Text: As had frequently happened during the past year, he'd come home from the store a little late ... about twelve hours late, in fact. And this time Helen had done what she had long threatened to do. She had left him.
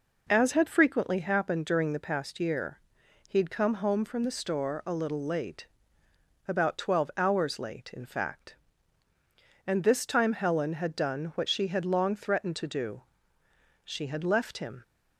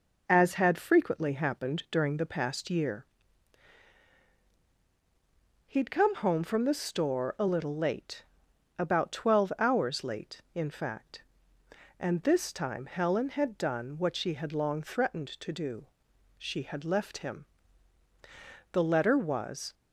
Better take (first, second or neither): first